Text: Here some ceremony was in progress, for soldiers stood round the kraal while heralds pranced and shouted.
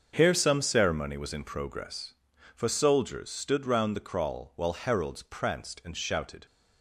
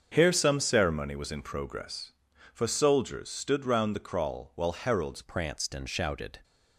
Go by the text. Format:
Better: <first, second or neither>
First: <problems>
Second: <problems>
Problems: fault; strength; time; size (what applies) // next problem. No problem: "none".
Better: first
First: starts louder than the rest; until 1.1 s; 7 dB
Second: starts louder than the rest; until 1.1 s; 7 dB // changes voice at "pranced"; from 5.2 s on; 1.1 s long